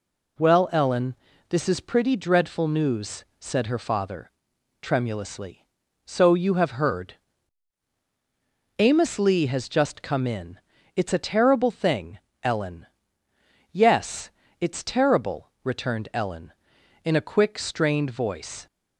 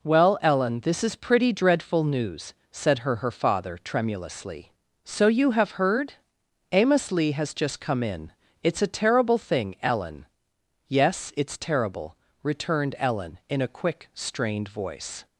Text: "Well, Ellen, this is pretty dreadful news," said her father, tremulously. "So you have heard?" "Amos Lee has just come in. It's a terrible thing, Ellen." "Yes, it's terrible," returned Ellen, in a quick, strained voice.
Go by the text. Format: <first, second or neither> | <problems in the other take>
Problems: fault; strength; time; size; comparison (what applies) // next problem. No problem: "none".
first | says "her" twice; at 3.1 s